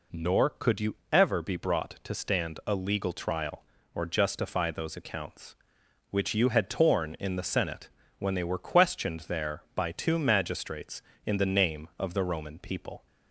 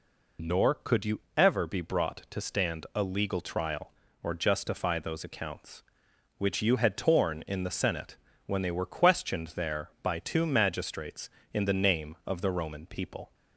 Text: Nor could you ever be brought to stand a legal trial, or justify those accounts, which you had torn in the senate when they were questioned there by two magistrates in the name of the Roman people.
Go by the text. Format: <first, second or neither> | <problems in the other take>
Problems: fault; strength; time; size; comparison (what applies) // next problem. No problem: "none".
first | loses the start of "Nor"; at 0.3 s; 30 ms // pauses between "you" and "ever"; slight; at 1.2 s; 0.16 s long; slight in the first // pauses between "senate" and "when"; slight; at 8.1 s; 0.30 s long; slight in the first